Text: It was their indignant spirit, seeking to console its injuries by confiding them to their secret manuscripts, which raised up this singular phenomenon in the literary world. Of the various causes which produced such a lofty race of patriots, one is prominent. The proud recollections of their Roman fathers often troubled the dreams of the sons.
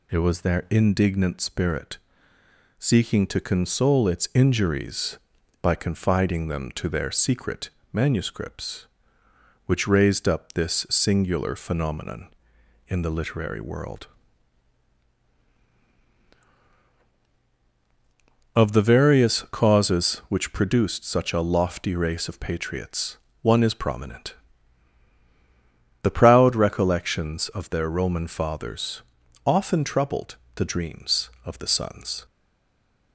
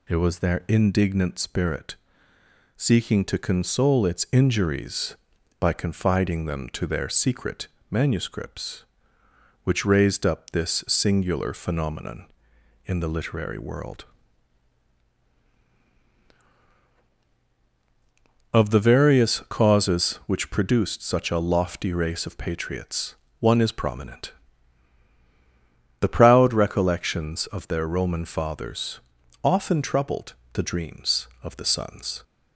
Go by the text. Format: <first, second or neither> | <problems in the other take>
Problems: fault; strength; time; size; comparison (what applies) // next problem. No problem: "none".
second | pauses between "secret" and "manuscripts"; slight; at 7.6 s; 0.24 s long; slight in the second // pauses between "fathers" and "often"; at 29.0 s; 0.44 s long; also in the second // pauses between "troubled" and "the"; slight; at 30.3 s; 0.20 s long; slight in the second // stays silent after the last word; slight; from 32.2 s on; 0.9 s long